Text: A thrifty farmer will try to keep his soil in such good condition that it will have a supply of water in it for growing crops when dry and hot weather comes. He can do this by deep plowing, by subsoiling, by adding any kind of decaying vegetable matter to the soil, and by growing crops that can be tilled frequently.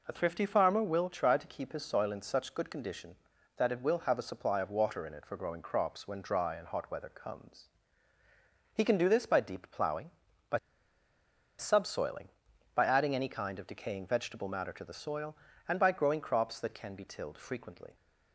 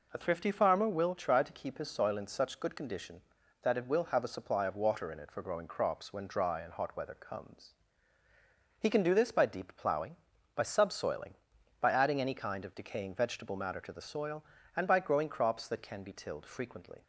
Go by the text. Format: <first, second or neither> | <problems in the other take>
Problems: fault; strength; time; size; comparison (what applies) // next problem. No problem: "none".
second | pauses between "by" and "subsoiling"; at 10.5 s; 1.0 s long